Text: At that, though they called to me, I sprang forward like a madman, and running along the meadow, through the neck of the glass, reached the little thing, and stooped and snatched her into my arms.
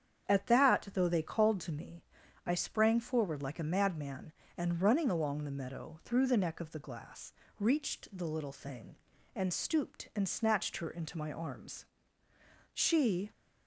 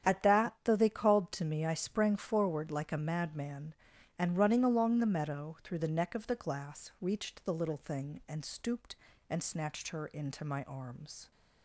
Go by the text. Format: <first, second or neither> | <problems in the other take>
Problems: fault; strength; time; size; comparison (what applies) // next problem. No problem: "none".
second | starts louder than the rest; strong; until 1.3 s; 8.5 dB; strong in the second // goes on to say "She"; from 12.7 s on; 0.58 s long